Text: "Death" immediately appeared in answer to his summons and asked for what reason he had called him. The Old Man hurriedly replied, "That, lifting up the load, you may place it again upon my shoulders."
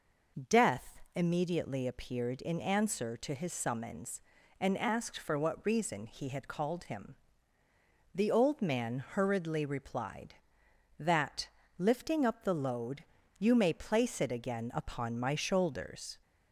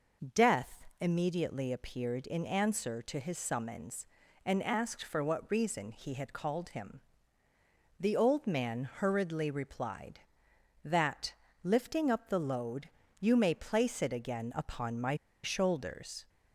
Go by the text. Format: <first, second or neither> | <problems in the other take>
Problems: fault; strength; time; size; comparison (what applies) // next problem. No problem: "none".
first | pauses between "my" and "shoulders"; slight; at 15.1 s; 0.29 s long